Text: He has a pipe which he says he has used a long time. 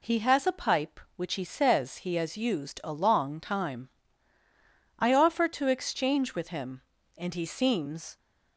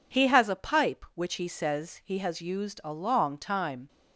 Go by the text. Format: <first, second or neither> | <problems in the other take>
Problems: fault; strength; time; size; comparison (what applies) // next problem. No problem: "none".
second | goes on to say "I offer to exchange with him and he seems"; strong; from 4.9 s on; 3.1 s long